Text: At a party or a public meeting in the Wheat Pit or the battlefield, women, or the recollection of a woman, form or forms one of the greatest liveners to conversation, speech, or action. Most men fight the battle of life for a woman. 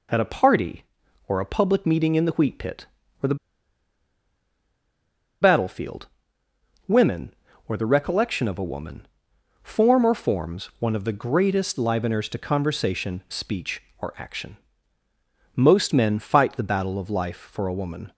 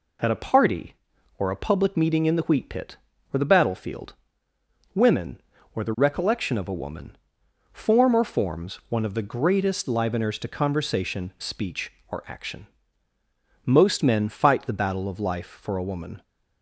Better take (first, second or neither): second